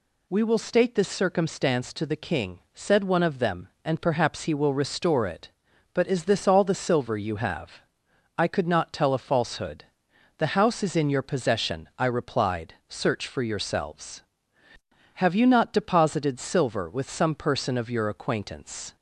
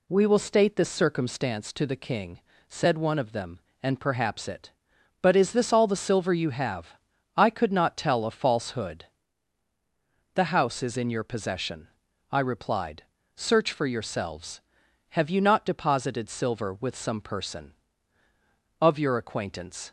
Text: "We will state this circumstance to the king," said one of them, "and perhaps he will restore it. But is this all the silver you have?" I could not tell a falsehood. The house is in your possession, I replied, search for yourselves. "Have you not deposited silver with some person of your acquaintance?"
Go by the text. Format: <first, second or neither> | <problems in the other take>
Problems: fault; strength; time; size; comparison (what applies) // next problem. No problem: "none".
first | skips "he will restore"; at 4.4 s